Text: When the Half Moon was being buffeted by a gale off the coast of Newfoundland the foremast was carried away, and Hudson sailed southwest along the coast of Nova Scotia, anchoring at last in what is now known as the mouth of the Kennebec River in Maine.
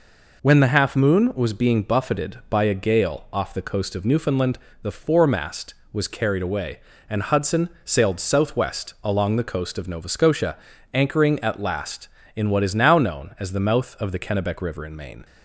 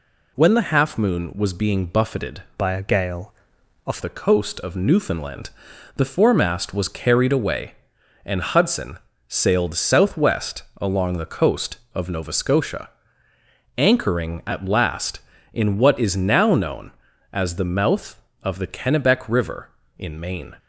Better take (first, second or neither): first